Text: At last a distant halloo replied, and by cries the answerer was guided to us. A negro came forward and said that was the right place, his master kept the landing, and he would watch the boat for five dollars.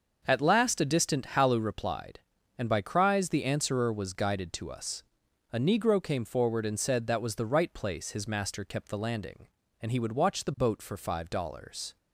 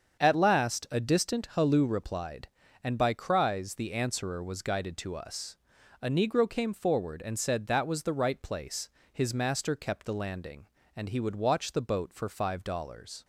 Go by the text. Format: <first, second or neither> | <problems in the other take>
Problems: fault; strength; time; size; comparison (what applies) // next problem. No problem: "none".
neither | starts louder than the rest; the same in both